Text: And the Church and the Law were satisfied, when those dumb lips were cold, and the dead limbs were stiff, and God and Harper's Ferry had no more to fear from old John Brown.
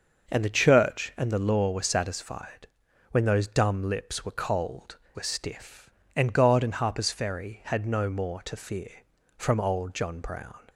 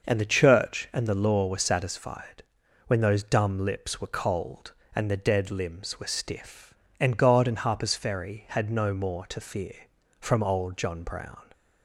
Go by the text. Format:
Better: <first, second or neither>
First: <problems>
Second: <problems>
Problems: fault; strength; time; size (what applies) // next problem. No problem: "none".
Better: second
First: starts louder than the rest; noticeable; until 1.3 s; 6 dB // skips "and the dead limbs"; at 5.0 s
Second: starts louder than the rest; noticeable; until 1.0 s; 6 dB